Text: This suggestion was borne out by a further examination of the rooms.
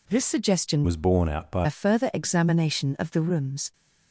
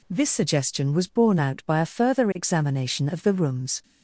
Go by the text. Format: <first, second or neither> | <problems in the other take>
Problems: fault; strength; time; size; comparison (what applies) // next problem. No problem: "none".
second | changes voice from "was" to "by"; from 0.8 to 1.6 s; 0.8 s long